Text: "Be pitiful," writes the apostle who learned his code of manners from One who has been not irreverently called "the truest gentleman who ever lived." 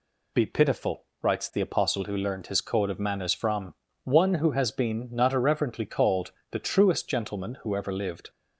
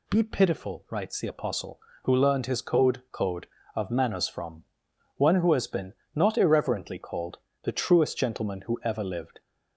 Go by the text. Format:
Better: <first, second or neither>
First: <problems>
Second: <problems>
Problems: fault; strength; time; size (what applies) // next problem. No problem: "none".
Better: first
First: pauses between "from" and "One"; slight; at 3.7 s; 0.30 s long // pauses between "called" and "the"; slight; at 6.3 s; 0.20 s long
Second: says "code" twice; at 3.1 s // pauses between "from" and "One"; noticeable; at 4.6 s; 0.52 s long // pauses between "been" and "not"; slight; at 5.9 s; 0.20 s long // pauses between "called" and "the"; slight; at 7.3 s; 0.24 s long